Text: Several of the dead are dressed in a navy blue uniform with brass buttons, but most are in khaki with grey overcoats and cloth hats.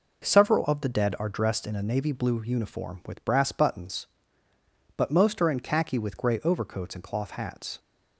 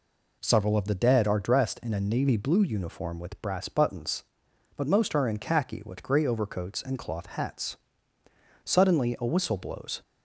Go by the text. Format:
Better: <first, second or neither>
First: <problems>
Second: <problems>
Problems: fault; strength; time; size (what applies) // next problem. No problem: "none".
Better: first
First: none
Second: goes on to say "Suddenly a whistle blows"; from 8.6 s on; 1.3 s long